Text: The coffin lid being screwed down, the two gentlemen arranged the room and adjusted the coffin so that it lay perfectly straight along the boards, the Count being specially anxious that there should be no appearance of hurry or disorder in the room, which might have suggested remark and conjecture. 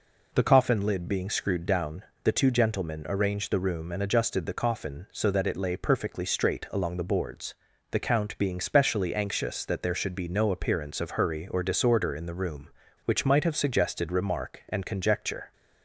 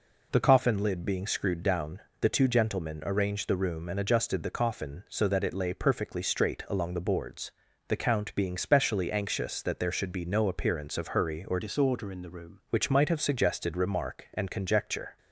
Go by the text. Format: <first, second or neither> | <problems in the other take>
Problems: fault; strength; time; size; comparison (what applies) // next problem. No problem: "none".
first | changes voice from "disorder" to "room"; from 11.6 to 12.6 s; 1.0 s long